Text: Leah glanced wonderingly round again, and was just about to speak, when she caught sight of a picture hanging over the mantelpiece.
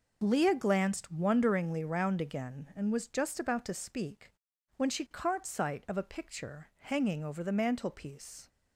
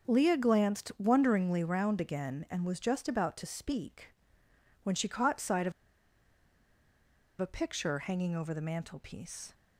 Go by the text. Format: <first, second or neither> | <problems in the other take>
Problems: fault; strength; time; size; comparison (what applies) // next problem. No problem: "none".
first | starts louder than the rest; until 1.1 s; 6.5 dB // pauses between "of" and "a"; strong; at 5.7 s; 1.6 s long